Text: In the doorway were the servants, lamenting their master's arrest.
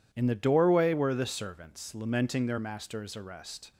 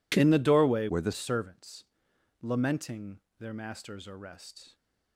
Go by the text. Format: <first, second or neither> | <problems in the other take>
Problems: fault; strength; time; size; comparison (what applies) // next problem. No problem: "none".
first | changes voice from "were" to "the"; from 0.8 to 1.1 s; 0.3 s long // pauses between "lamenting" and "their"; slight; at 3.2 s; 0.18 s long